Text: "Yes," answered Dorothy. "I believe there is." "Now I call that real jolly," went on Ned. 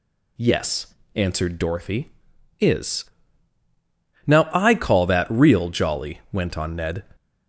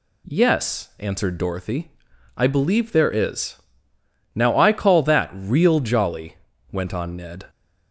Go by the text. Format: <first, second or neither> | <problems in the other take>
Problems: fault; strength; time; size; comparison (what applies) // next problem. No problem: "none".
second | skips "I believe there"; at 2.3 s